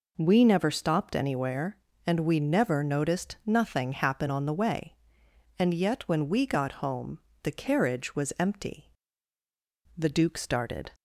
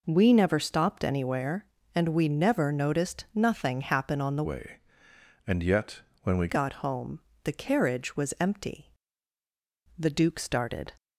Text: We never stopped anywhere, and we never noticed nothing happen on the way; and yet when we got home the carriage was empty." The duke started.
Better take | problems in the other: first | changes voice from "way" to "we"; from 4.4 to 6.4 s; 2.0 s long // pauses between "yet" and "when"; slight; at 6.0 s; 0.22 s long // pauses between "home" and "the"; slight; at 7.1 s; 0.24 s long; slight in the first

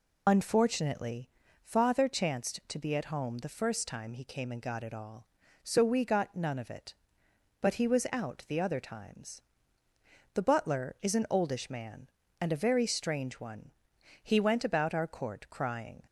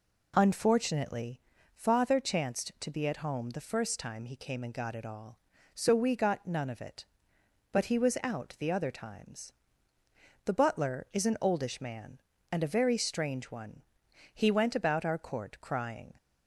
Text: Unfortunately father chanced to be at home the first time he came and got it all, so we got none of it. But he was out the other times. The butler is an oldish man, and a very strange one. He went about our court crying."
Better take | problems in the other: second | loses the start of "Unfortunately"; at 0.2 s; 45 ms // pauses between "Unfortunately" and "father"; at 1.2 s; 0.36 s long; slight in the second

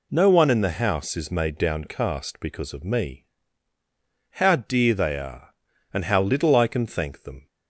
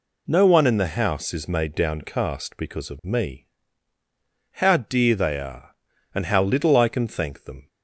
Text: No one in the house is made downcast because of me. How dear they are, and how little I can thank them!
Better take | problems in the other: neither | none

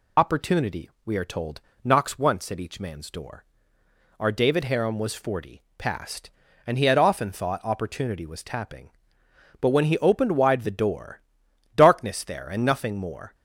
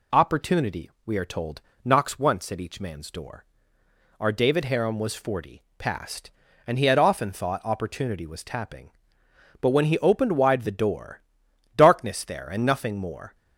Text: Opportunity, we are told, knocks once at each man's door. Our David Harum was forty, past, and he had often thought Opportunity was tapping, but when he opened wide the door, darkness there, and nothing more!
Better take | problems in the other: second | loses the start of "Opportunity"; at 0.1 s; 50 ms

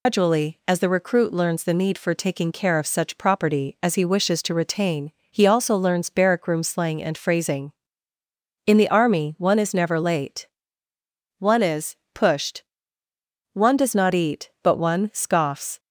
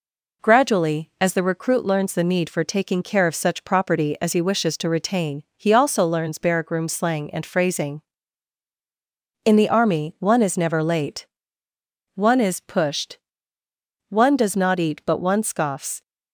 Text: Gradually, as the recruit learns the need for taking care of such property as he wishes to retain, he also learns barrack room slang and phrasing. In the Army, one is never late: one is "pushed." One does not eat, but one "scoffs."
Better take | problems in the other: second | loses the start of "Gradually"; at 0.0 s; 180 ms // pauses between "is" and "pushed"; slight; at 11.9 s; 0.20 s long

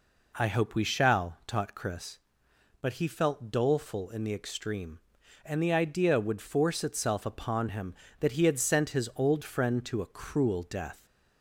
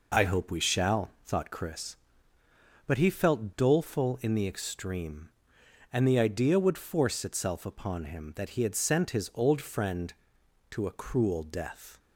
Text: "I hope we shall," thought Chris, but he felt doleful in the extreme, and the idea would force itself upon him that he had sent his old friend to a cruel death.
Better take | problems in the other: second | says "taught" for "thought"; at 1.4 s

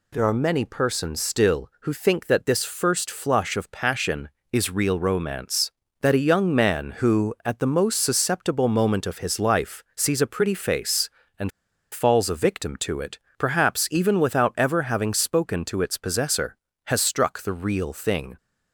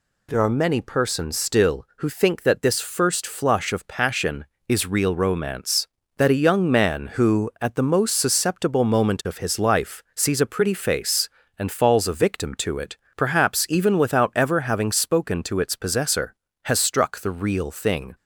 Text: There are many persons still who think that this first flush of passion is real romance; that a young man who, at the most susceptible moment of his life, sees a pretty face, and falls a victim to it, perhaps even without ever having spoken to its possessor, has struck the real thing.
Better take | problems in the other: second | pauses between "and" and "falls"; at 11.5 s; 0.42 s long

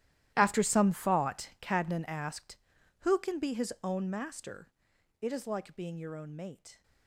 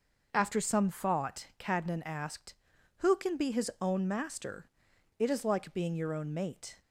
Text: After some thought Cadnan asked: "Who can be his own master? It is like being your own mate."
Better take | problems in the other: second | gets quieter; strong; throughout; 18.5 dB

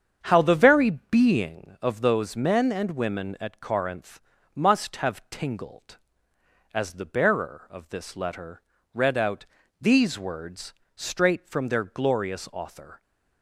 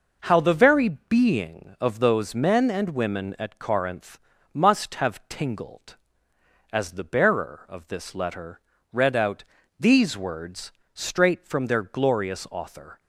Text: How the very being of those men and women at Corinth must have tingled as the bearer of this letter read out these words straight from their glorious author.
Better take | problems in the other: second | starts louder than the rest; strong; until 1.7 s; 7.5 dB // pauses between "Corinth" and "must"; slight; at 4.2 s; 0.34 s long; slight in the second // pauses between "letter" and "read"; slight; at 8.6 s; 0.32 s long; slight in the second // pauses between "out" and "these"; slight; at 9.4 s; 0.36 s long; slight in the second // pauses between "words" and "straight"; slight; at 10.7 s; 0.22 s long; slight in the second

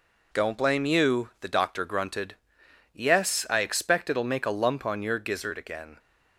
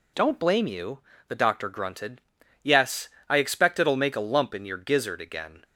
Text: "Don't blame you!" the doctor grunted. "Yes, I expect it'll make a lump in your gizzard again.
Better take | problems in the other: second | says "on" for "in"; at 4.8 s

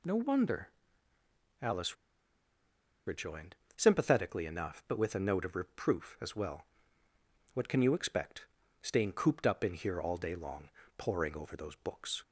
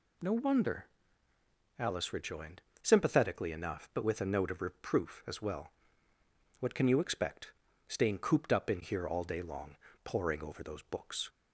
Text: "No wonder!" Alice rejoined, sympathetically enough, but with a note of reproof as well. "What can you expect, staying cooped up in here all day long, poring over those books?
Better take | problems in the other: second | pauses between "Alice" and "rejoined"; at 1.9 s; 1.1 s long

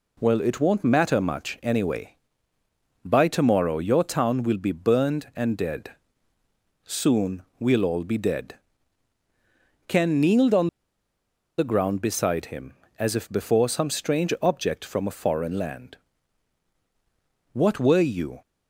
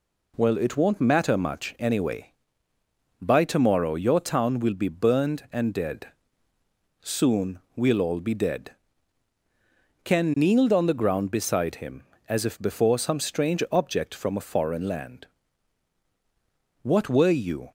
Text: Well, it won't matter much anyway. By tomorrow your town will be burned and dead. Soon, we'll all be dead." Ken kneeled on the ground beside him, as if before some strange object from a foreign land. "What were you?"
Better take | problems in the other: second | pauses between "on" and "the"; noticeable; at 10.6 s; 0.89 s long

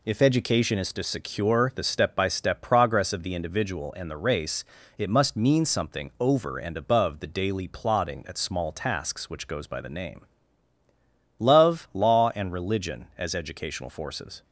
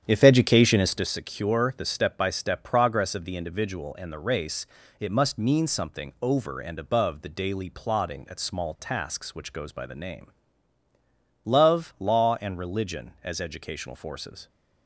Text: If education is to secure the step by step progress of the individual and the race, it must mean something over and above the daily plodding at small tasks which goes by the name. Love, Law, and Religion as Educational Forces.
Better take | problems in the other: first | starts louder than the rest; strong; until 1.2 s; 9 dB

